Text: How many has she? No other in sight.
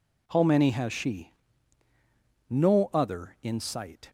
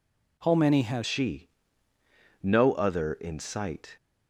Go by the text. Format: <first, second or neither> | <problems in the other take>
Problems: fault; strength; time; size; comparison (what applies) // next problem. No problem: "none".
first | changes voice at "she"; from 1.0 s on; 2.9 s long